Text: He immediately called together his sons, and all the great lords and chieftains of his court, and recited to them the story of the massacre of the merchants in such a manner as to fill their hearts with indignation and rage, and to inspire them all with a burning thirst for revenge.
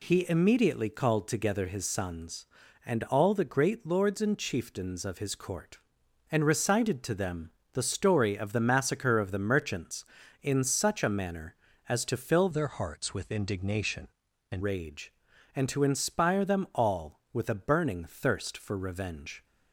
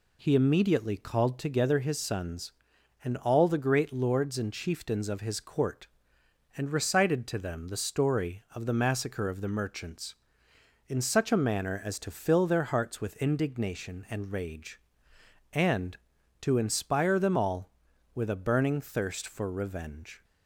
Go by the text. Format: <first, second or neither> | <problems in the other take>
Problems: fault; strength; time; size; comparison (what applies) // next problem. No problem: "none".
second | pauses between "them" and "the"; slight; at 7.5 s; 0.20 s long // changes voice from "their" to "and"; from 12.5 to 14.6 s; 2.1 s long